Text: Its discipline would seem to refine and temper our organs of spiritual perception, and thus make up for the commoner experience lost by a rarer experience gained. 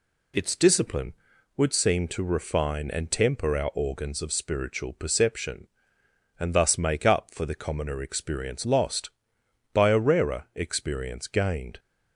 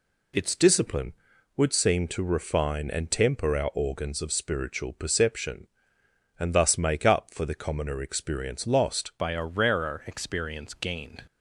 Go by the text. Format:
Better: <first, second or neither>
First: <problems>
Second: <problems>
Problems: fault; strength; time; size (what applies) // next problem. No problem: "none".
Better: first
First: none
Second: changes voice at "by"; from 9.1 s on; 2.1 s long